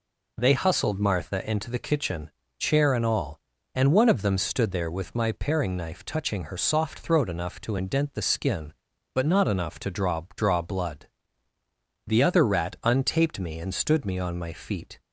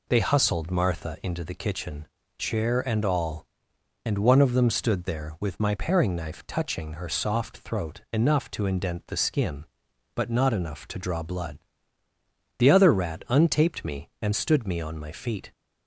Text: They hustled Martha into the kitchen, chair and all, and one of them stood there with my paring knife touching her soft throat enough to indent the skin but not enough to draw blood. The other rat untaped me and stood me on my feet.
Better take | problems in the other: second | says "draw" twice; at 10.3 s

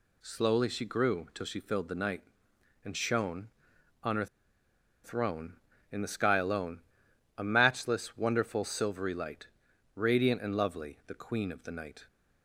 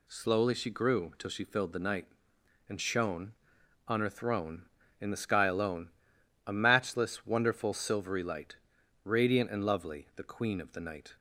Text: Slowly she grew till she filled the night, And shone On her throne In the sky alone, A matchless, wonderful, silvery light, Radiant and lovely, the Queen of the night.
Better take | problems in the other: second | pauses between "her" and "throne"; noticeable; at 4.2 s; 0.78 s long

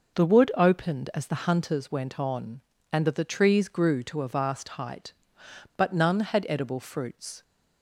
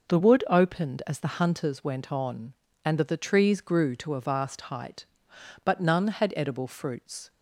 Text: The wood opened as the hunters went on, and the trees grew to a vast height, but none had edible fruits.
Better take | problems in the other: neither | none

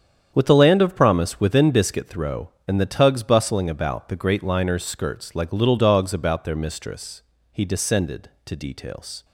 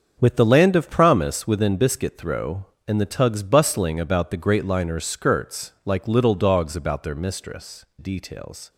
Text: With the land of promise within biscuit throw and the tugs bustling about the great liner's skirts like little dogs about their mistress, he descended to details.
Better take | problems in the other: first | starts louder than the rest; until 1.2 s; 7 dB; strong in the first // skips "he descended to"; at 7.9 s

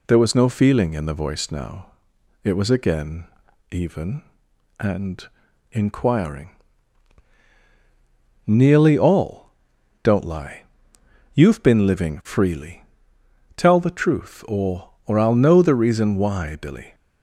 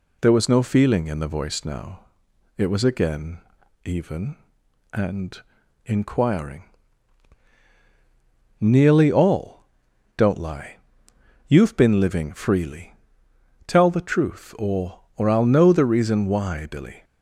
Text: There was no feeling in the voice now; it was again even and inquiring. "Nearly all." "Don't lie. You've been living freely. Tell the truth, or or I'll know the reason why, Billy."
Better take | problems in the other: neither | pauses between "again" and "even"; noticeable; the same in both // pauses between "and" and "inquiring"; the same in both

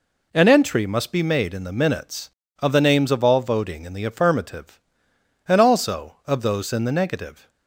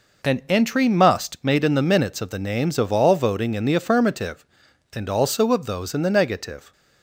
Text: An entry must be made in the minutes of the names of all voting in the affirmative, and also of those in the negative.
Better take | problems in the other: first | skips "be"; at 1.4 s

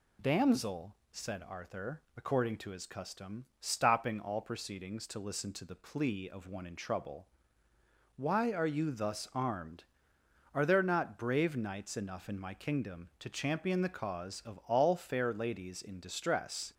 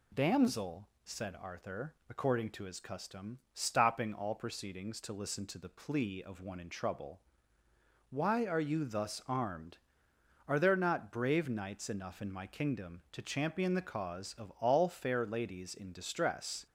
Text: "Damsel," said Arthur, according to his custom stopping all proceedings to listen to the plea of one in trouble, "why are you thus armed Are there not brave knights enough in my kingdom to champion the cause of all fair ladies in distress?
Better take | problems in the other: neither | pauses between "custom" and "stopping"; slight; the same in both

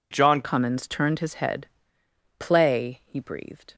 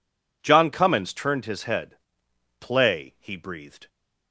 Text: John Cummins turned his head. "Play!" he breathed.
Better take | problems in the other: second | changes voice at "Cummins"; from 0.4 s on; 3.3 s long

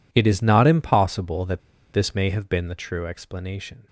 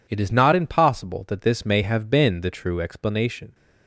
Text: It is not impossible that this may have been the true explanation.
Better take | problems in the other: second | pauses between "that" and "this"; slight; at 1.6 s; 0.32 s long

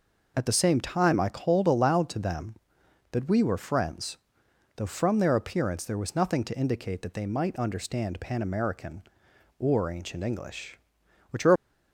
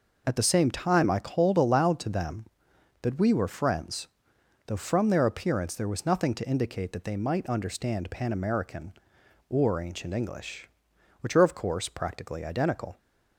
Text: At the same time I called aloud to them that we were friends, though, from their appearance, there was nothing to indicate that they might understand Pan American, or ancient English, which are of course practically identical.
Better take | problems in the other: second | stops before "of course practically identical"; at 11.5 s

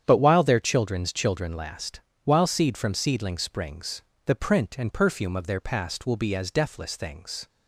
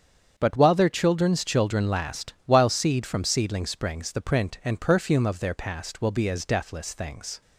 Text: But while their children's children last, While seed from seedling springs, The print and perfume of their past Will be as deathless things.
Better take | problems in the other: neither | starts louder than the rest; strong; the same in both

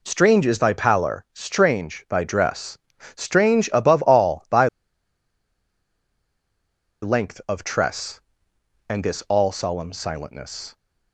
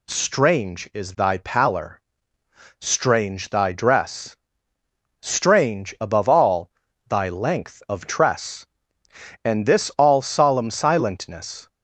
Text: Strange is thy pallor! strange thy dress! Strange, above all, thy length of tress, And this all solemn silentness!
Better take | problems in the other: second | pauses between "thy" and "length"; strong; at 4.6 s; 2.3 s long

